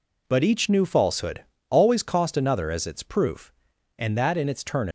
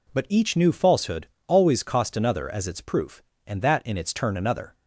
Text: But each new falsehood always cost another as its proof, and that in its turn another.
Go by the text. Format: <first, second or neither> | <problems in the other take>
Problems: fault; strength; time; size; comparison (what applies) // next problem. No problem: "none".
second | pauses between "falsehood" and "always"; slight; at 1.4 s; 0.24 s long; slight in the second // stops before "another"; at 4.8 s